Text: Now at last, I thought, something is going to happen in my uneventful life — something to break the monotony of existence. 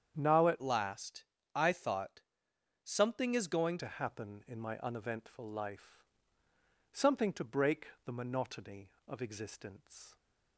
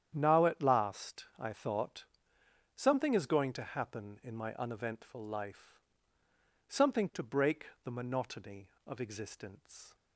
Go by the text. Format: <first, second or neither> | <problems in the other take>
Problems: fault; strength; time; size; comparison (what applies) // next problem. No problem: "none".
second | starts louder than the rest; strong; until 1.1 s; 8.5 dB; strong in the second // changes voice from "last" to "going"; from 0.6 to 3.7 s; 3.1 s long // pauses between "break" and "the"; slight; at 7.8 s; 0.18 s long; slight in the second